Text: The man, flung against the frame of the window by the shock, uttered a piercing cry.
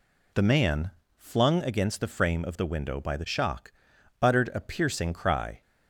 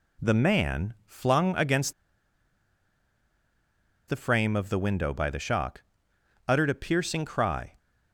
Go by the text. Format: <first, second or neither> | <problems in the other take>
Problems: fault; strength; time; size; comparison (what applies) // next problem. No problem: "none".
first | pauses between "against" and "the"; strong; at 1.9 s; 2.1 s long